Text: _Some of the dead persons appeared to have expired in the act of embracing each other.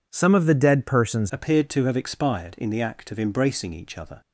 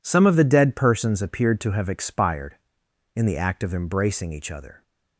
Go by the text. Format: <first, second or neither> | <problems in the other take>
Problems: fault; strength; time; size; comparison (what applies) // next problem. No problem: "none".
second | changes voice at "appeared"; from 1.3 s on; 2.9 s long